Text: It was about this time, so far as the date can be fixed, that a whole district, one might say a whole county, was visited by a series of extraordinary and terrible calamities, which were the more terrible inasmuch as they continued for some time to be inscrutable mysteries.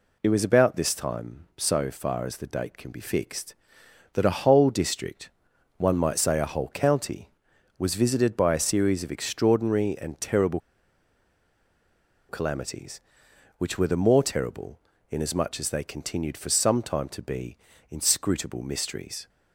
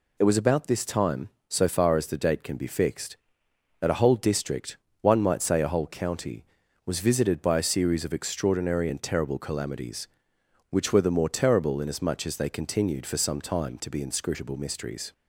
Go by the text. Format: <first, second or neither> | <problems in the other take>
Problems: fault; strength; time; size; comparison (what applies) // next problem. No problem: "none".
second | pauses between "terrible" and "calamities"; strong; at 10.5 s; 1.7 s long // pauses between "terrible" and "inasmuch"; slight; at 14.8 s; 0.30 s long // pauses between "be" and "inscrutable"; slight; at 17.5 s; 0.32 s long